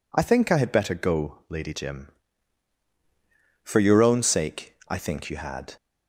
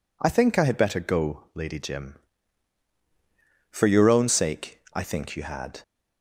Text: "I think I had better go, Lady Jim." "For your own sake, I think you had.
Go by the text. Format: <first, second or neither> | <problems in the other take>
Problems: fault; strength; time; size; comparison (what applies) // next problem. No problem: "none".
neither | none